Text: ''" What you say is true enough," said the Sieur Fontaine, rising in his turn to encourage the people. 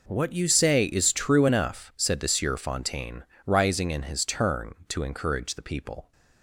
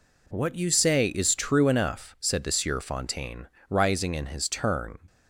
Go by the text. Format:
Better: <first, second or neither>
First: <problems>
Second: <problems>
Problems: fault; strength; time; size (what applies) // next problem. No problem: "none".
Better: first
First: none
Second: stops before "to encourage the people"; at 5.0 s